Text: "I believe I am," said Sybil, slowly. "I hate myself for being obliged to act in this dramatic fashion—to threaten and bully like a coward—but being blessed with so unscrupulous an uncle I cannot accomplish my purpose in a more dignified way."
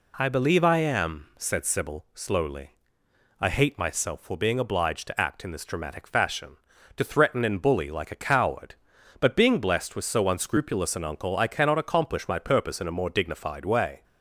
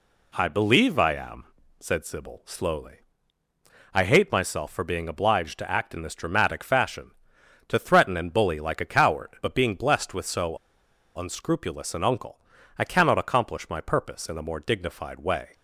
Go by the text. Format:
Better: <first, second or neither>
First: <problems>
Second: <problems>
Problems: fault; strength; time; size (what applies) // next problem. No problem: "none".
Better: first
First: none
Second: pauses between "so" and "unscrupulous"; noticeable; at 10.5 s; 0.58 s long // pauses between "uncle" and "I"; slight; at 12.4 s; 0.36 s long